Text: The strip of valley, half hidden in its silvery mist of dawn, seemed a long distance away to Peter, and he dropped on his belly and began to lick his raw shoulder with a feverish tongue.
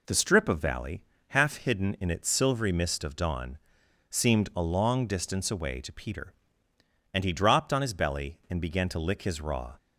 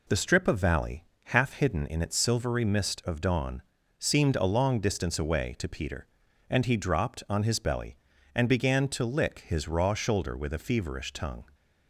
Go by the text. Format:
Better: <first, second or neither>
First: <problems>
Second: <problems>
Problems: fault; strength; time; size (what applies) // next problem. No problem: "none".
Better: second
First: stops before "shoulder with a feverish tongue"; at 9.7 s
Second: none